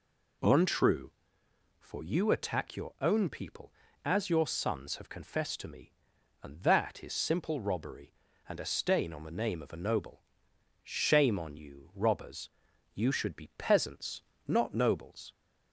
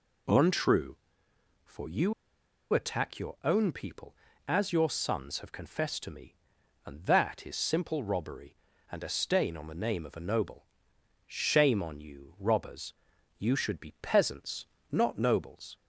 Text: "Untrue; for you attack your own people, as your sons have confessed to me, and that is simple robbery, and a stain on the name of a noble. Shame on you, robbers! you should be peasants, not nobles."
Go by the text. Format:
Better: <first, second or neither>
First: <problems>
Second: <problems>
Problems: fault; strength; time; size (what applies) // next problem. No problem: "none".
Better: first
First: none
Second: pauses between "you" and "attack"; noticeable; at 2.1 s; 0.60 s long